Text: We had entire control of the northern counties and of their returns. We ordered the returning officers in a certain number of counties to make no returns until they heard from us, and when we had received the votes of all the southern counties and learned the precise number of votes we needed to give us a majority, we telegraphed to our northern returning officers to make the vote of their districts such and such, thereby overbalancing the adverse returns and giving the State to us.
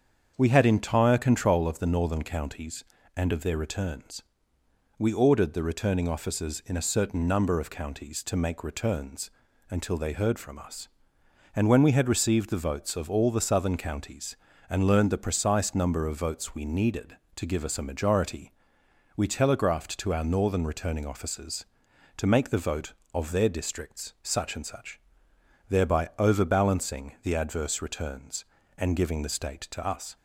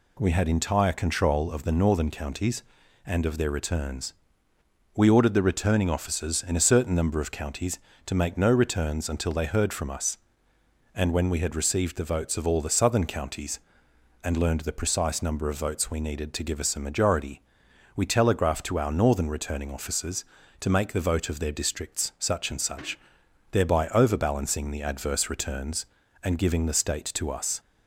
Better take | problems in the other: second | starts louder than the rest; strong; until 1.3 s; 7 dB // skips "no"; at 8.6 s // pauses between "returns" and "until"; at 9.2 s; 0.40 s long

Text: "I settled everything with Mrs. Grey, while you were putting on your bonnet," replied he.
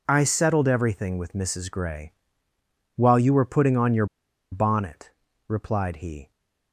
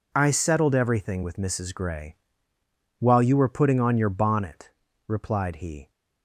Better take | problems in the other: second | pauses between "your" and "bonnet"; noticeable; at 4.0 s; 0.46 s long

